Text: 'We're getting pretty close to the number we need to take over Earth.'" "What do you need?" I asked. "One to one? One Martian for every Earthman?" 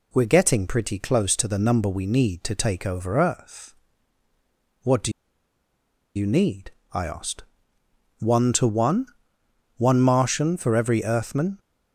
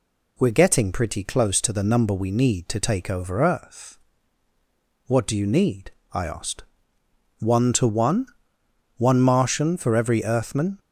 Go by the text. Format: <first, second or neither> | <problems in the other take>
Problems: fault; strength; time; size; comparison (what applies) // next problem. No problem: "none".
second | pauses between "do" and "you"; at 5.1 s; 1.0 s long